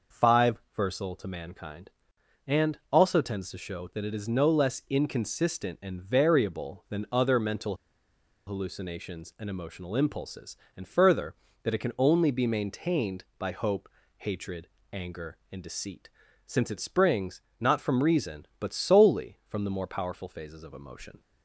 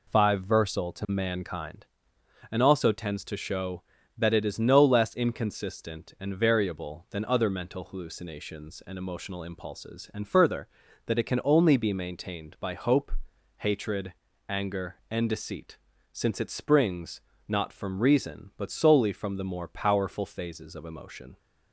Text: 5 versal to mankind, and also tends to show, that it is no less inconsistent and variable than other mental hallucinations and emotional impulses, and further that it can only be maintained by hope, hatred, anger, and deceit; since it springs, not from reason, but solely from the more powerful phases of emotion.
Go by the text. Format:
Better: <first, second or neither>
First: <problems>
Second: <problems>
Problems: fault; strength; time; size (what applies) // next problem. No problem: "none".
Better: second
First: pauses between "mental" and "hallucinations"; noticeable; at 7.7 s; 0.71 s long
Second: none